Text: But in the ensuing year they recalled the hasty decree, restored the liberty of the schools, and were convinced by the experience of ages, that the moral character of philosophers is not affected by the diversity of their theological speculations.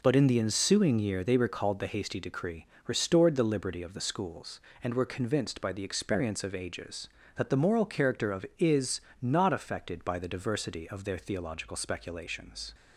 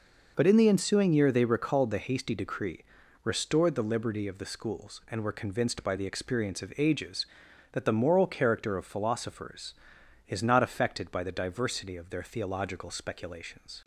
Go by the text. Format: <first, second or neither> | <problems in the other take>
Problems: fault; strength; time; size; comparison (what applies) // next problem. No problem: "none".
second | skips "philosophers"; at 8.5 s // pauses between "is" and "not"; slight; at 9.0 s; 0.18 s long